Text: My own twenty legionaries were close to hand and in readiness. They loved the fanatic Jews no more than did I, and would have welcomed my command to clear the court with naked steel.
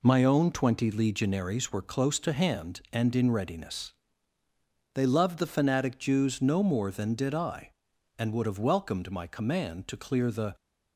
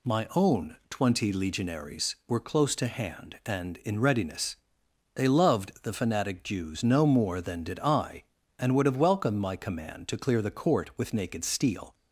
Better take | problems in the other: second | stops before "court with naked steel"; at 10.5 s

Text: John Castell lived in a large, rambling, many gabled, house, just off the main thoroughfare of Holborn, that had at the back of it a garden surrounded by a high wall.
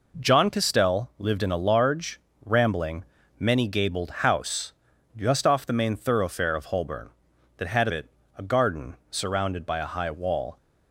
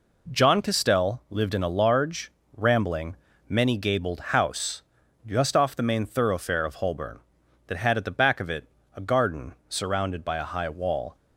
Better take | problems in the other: second | skips "at the back of"; at 7.8 s // pauses between "it" and "a"; slight; at 8.0 s; 0.30 s long; slight in the second // pauses between "garden" and "surrounded"; slight; at 8.9 s; 0.16 s long; slight in the second

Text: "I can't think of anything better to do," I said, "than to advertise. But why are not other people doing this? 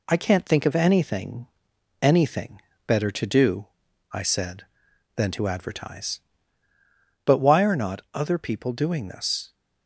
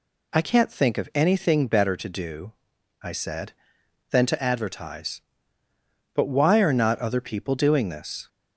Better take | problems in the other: second | says "anything" twice; at 2.0 s

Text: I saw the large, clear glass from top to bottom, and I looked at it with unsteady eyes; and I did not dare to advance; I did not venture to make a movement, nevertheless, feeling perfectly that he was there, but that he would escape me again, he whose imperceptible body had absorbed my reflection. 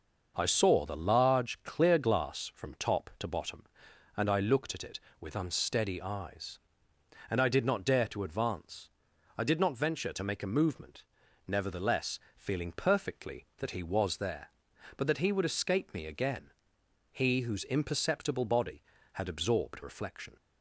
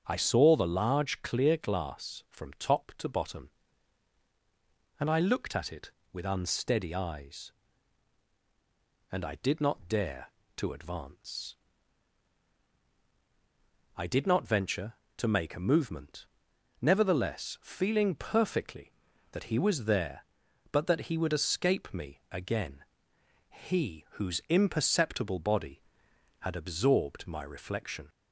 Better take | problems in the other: second | starts louder than the rest; until 1.3 s; 6 dB; strong in the second // skips "my"; at 19.8 s

